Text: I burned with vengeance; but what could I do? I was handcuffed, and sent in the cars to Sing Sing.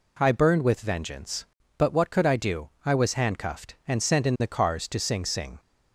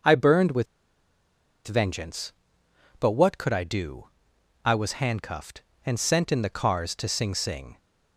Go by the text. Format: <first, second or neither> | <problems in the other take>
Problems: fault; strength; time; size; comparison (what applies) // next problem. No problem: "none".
first | pauses between "with" and "vengeance"; at 0.6 s; 1.0 s long